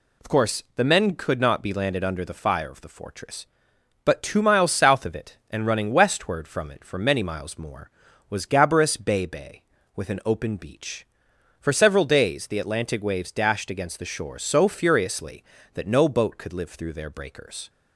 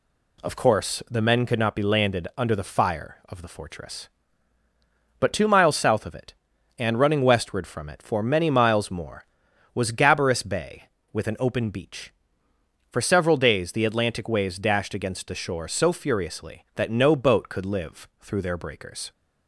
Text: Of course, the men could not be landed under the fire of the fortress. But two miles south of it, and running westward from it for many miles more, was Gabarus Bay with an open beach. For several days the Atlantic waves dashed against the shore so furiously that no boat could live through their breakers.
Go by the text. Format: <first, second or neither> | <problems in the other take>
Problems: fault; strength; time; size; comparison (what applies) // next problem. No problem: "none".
second | says "Bay" twice; at 9.2 s